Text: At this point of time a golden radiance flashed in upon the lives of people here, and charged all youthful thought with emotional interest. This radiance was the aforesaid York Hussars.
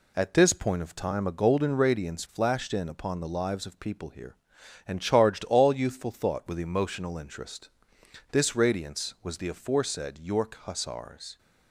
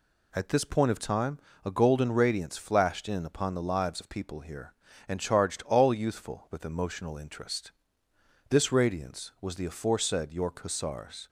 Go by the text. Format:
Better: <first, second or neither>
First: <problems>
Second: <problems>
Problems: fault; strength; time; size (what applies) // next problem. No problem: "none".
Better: first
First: none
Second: pauses between "time" and "a"; slight; at 1.3 s; 0.26 s long // skips "thought"; at 6.4 s